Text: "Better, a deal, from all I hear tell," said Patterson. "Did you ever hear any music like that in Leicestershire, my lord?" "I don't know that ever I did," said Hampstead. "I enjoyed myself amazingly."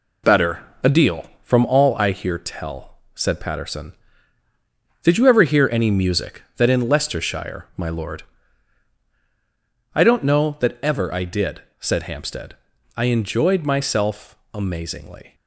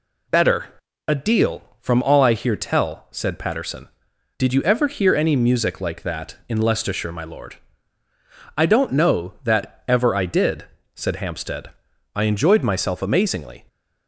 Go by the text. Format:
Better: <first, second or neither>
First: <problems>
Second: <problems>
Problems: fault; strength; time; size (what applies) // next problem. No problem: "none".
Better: second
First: skips "like"; at 6.4 s // pauses between "myself" and "amazingly"; slight; at 14.3 s; 0.20 s long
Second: none